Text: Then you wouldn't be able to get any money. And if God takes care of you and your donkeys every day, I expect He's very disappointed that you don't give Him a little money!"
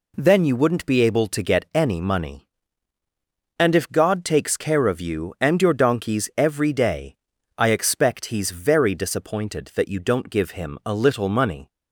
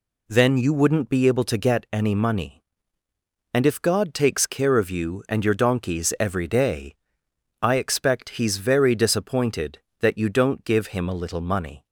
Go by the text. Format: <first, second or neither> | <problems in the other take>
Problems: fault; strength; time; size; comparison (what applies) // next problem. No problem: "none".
neither | none